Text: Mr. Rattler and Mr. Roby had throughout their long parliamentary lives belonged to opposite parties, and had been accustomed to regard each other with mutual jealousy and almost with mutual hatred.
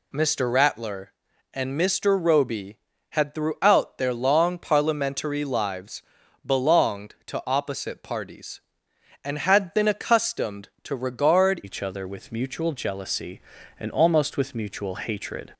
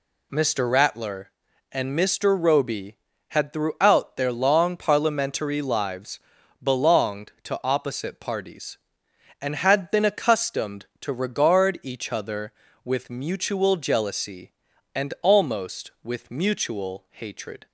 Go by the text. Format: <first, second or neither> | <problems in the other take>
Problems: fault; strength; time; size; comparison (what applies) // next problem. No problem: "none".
second | pauses between "lives" and "belonged"; at 6.0 s; 0.44 s long; also in the second // changes voice at "each"; from 11.6 s on; 3.9 s long